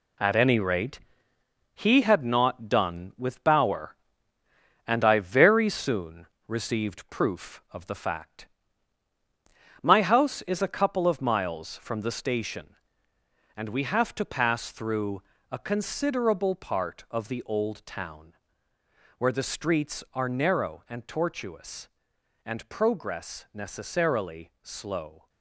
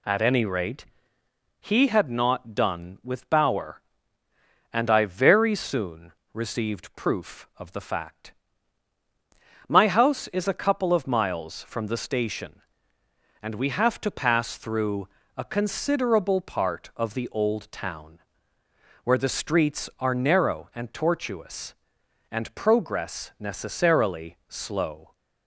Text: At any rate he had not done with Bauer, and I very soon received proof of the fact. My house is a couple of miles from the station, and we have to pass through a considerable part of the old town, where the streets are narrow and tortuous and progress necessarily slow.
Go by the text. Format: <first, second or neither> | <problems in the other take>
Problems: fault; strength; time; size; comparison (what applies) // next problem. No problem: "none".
second | gets quieter; strong; throughout; 7.5 dB // pauses between "rate" and "he"; noticeable; at 0.9 s; 0.76 s long; noticeable in the second // pauses between "soon" and "received"; slight; at 6.2 s; 0.22 s long; slight in the second // pauses between "through" and "a"; slight; at 15.2 s; 0.30 s long; slight in the second